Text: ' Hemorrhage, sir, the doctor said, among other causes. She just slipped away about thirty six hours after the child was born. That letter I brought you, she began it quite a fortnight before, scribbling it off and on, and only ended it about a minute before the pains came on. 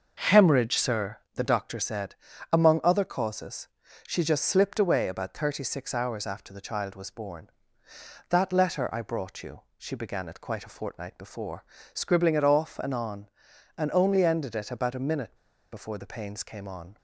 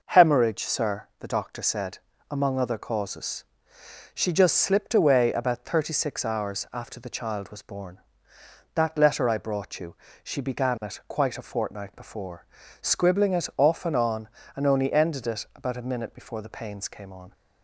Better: second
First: starts louder than the rest; noticeable; until 1.1 s; 6 dB // pauses between "minute" and "before"; slight; at 15.3 s; 0.36 s long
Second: none

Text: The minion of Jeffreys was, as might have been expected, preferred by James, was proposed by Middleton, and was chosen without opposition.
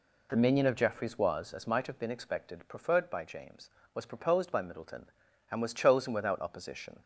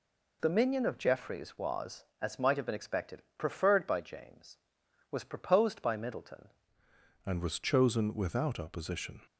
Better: first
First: none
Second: changes voice at "and"; from 7.2 s on; 2.0 s long

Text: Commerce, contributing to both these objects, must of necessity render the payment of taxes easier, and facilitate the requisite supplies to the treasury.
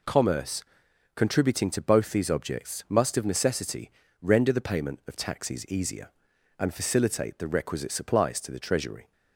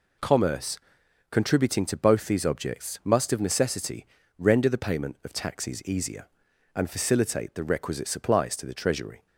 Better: neither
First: pauses between "necessity" and "render"; slight; at 3.8 s; 0.30 s long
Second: pauses between "necessity" and "render"; slight; at 4.0 s; 0.32 s long

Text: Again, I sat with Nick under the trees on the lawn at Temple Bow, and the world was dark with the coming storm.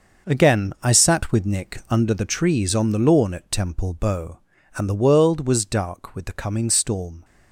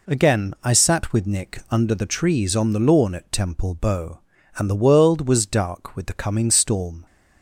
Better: second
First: gets quieter; strong; throughout; 10 dB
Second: none

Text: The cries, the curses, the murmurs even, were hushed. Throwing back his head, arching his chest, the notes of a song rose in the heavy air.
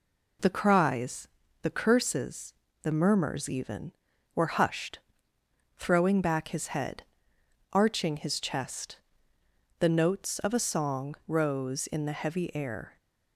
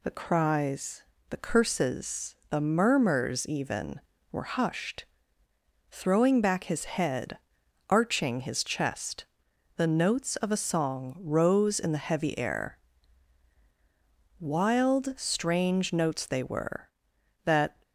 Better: first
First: none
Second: goes on to say "Wild strange notes they were that"; strong; from 14.3 s on; 3.4 s long

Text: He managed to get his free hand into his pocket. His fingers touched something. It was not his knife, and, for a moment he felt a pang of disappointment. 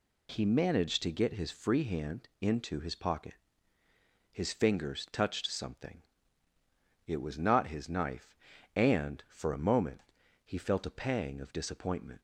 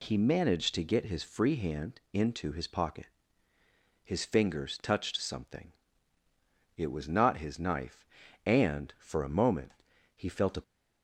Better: first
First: pauses between "moment" and "he"; at 10.0 s; 0.44 s long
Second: pauses between "moment" and "he"; at 9.7 s; 0.44 s long // stops before "pang of disappointment"; at 10.6 s

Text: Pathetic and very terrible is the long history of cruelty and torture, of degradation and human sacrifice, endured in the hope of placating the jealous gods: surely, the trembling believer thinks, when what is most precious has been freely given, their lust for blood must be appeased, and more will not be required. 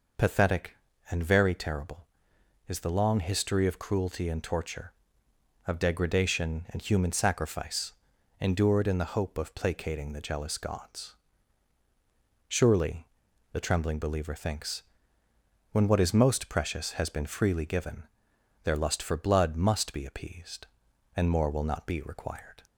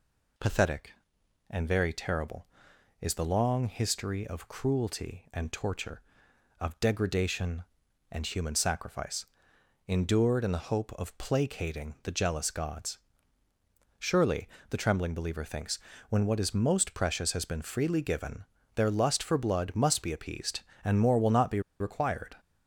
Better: first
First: none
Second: pauses between "be" and "required"; slight; at 21.6 s; 0.18 s long

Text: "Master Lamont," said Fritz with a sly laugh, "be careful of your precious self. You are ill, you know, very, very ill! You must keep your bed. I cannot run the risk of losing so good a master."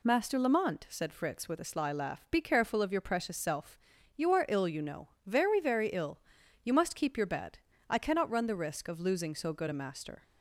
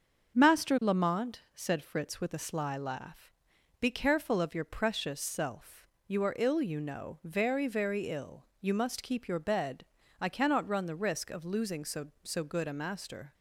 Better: first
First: none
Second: starts louder than the rest; until 1.4 s; 6.5 dB // says "so" twice; at 12.2 s

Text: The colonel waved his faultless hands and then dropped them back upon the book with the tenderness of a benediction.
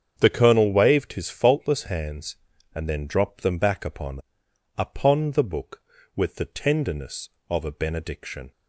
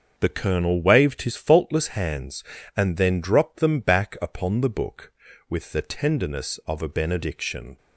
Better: second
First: starts louder than the rest; strong; until 1.1 s; 7.5 dB // says "upon" twice; at 4.7 s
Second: starts louder than the rest; until 1.1 s; 6.5 dB

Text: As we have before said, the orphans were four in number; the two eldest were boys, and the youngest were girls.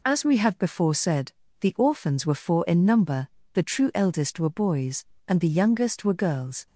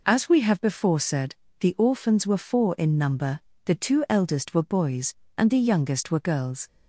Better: second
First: says "true" for "two"; at 3.6 s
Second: none

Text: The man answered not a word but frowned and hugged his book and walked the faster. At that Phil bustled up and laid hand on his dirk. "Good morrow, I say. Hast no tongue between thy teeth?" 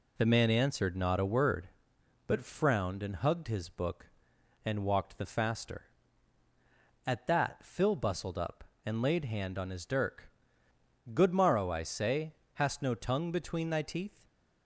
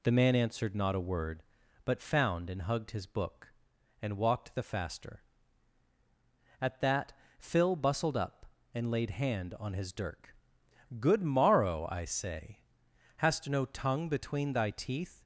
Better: first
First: none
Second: says "found" for "frowned"; at 1.9 s // pauses between "that" and "Phil"; slight; at 7.1 s; 0.28 s long

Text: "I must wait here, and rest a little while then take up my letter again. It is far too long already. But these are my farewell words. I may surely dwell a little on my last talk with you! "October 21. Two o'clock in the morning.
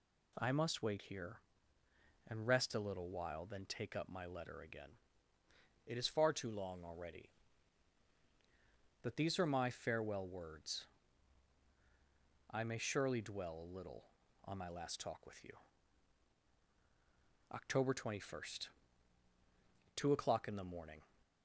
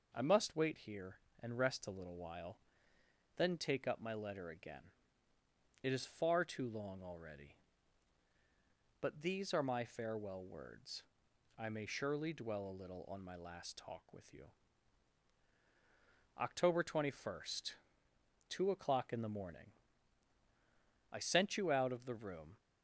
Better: first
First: none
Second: pauses between "while" and "then"; noticeable; at 2.5 s; 0.78 s long // goes on to say "I sent you out of the room"; from 21.0 s on; 1.4 s long

